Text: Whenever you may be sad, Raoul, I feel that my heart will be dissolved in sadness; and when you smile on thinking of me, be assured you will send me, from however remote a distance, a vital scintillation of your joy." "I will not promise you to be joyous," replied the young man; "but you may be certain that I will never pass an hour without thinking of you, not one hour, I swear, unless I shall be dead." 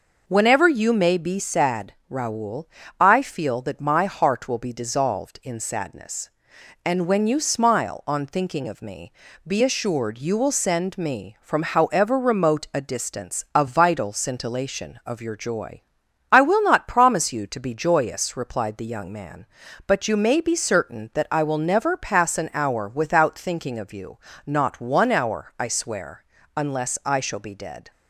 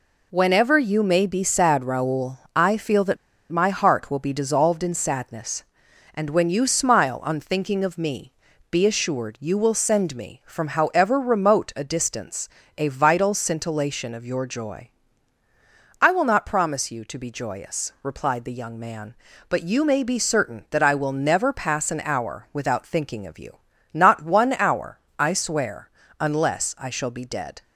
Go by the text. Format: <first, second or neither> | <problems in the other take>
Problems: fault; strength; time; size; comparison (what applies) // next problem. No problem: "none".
first | pauses between "that" and "my"; slight; at 3.1 s; 0.34 s long